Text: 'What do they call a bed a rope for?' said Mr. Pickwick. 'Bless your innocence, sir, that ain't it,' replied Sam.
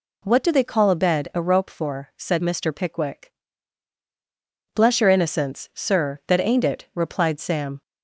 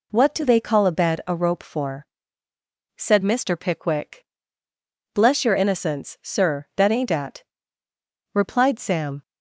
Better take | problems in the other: first | says "at" for "it"; at 7.1 s

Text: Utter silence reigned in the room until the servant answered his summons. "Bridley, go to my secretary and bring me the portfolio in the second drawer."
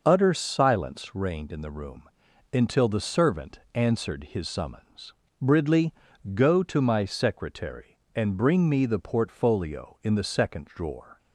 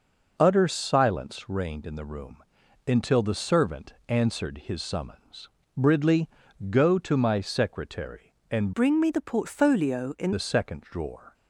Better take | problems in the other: first | pauses between "room" and "until"; at 2.4 s; 0.44 s long; also in the first // changes voice from "bring" to "in"; from 8.7 to 10.3 s; 1.6 s long

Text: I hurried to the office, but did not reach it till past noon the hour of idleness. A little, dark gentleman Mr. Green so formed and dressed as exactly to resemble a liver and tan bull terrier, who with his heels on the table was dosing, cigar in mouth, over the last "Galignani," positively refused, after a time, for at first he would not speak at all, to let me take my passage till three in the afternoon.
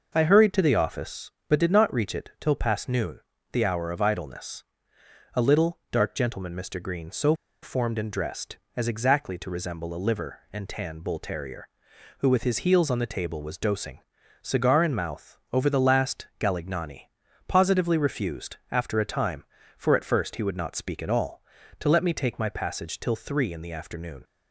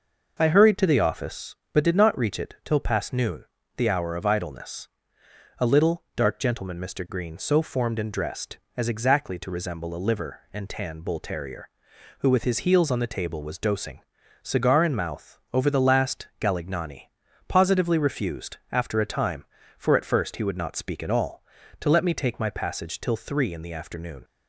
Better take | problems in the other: second | pauses between "noon" and "the"; slight; at 3.2 s; 0.30 s long; slight in the second // pauses between "so" and "formed"; slight; at 7.3 s; 0.29 s long

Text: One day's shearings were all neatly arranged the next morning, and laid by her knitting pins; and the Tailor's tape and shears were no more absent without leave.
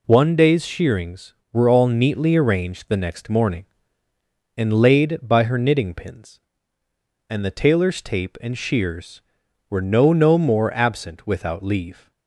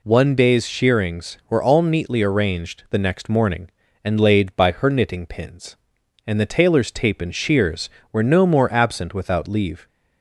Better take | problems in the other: second | says "no" twice; at 10.1 s

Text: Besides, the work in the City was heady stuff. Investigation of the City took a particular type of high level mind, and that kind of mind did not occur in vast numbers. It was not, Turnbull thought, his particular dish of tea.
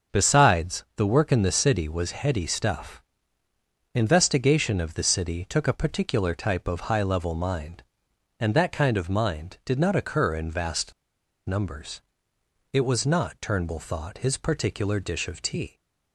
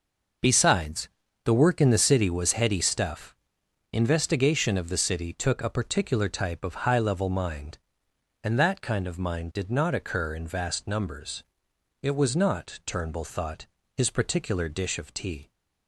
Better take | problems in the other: second | starts louder than the rest; until 1.2 s; 6.5 dB // pauses between "vast" and "numbers"; noticeable; at 10.9 s; 0.56 s long

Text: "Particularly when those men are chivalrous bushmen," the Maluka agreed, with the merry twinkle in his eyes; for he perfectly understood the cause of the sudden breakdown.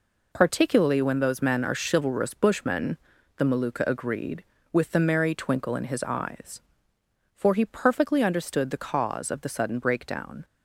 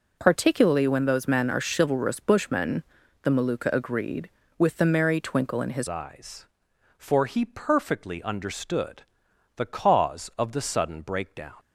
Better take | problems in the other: first | changes voice at "eyes"; from 5.8 s on; 5.7 s long // pauses between "understood" and "the"; noticeable; at 9.0 s; 0.52 s long

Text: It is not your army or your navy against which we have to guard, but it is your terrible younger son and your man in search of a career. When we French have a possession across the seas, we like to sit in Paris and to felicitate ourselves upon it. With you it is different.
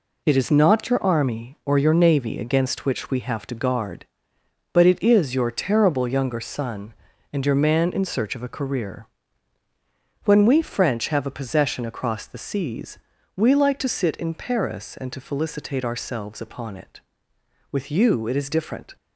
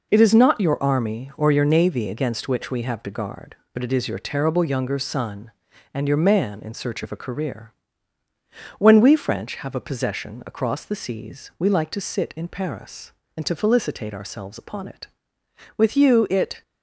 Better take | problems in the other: first | stops before "is different"; at 16.6 s

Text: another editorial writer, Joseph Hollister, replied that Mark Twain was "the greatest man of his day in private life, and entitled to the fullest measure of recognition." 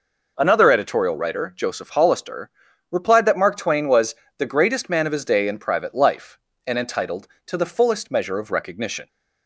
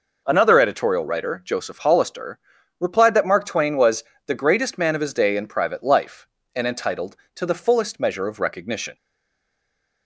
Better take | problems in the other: first | pauses between "was" and "the"; slight; at 4.0 s; 0.22 s long; slight in the first // stays silent after the last word; from 8.9 s on; 1.1 s long

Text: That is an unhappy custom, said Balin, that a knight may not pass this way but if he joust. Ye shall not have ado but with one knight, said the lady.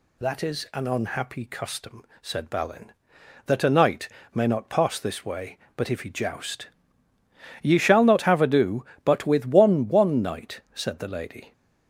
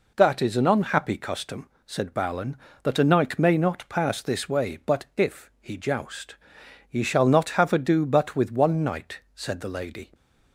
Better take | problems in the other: second | pauses between "knight" and "may"; slight; at 4.0 s; 0.26 s long // says "one" twice; at 9.8 s

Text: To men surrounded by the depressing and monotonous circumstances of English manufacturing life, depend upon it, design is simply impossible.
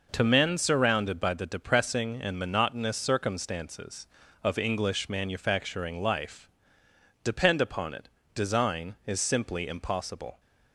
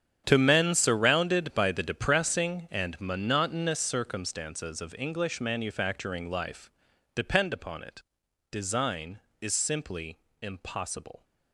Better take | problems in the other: first | gets quieter; strong; throughout; 15 dB // pauses between "simply" and "impossible"; slight; at 10.1 s; 0.22 s long

